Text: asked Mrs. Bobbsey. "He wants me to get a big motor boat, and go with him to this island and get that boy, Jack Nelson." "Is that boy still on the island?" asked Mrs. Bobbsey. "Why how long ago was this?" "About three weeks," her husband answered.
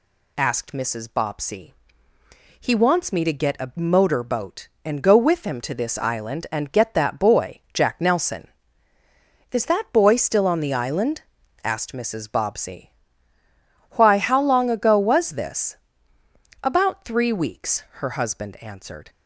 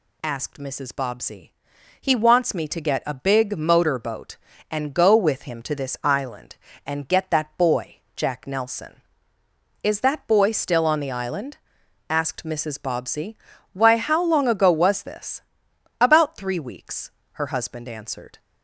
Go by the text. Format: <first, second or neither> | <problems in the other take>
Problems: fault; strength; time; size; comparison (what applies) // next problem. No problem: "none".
second | skips "big"; at 3.7 s